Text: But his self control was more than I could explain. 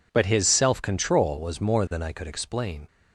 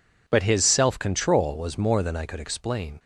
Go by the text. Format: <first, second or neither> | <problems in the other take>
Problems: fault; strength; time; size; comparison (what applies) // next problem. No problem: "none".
neither | none